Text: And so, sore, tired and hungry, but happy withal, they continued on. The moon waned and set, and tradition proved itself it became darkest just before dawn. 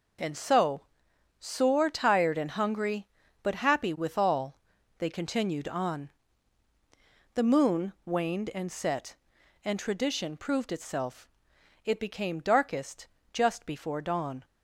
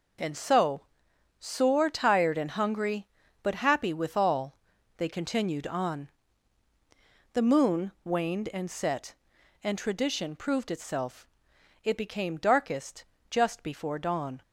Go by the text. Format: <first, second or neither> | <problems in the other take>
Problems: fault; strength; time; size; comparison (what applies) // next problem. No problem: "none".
neither | pauses between "itself" and "it"; noticeable; the same in both // pauses between "darkest" and "just"; slight; the same in both